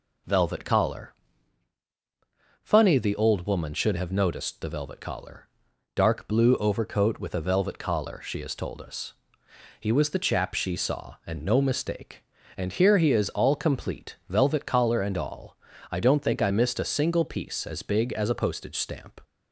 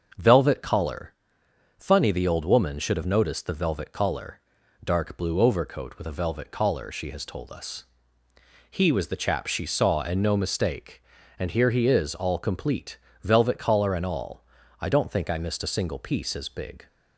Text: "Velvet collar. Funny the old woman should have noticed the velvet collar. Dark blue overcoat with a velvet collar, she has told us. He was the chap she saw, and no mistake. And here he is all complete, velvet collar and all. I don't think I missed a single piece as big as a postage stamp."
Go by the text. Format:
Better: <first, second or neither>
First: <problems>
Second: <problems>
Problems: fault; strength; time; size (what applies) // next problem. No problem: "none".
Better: first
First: none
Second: starts louder than the rest; until 1.8 s; 6.5 dB // stops before "as a postage stamp"; at 16.8 s